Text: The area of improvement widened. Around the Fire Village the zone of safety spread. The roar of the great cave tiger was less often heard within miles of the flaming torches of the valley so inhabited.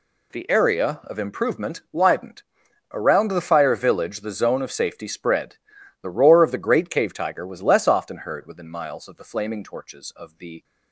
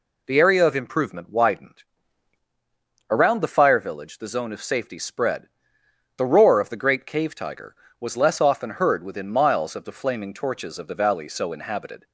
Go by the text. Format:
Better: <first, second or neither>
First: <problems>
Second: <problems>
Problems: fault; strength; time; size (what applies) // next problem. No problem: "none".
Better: second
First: stops before "valley so inhabited"; at 10.6 s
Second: none